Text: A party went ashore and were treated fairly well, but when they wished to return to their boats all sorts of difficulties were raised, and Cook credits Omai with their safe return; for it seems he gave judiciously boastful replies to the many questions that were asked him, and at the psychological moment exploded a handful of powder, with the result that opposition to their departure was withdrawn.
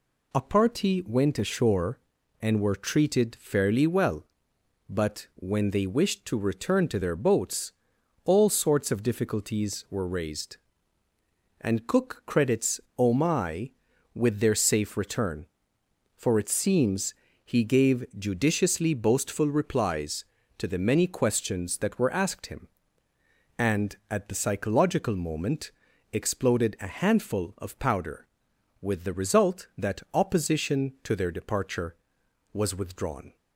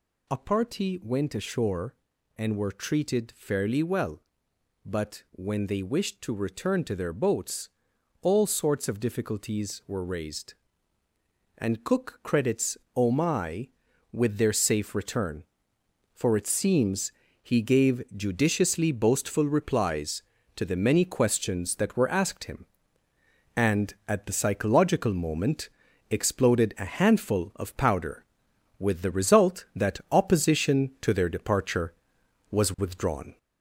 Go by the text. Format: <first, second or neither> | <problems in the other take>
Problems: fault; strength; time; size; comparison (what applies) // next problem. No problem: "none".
first | gets louder; noticeable; throughout; 4 dB // pauses between "boats" and "all"; noticeable; at 7.6 s; 0.52 s long; noticeable in the first // pauses between "credits" and "Omai"; slight; at 12.7 s; 0.18 s long; slight in the first // pauses between "seems" and "he"; slight; at 17.1 s; 0.30 s long; slight in the first // pauses between "moment" and "exploded"; at 25.6 s; 0.42 s long; also in the first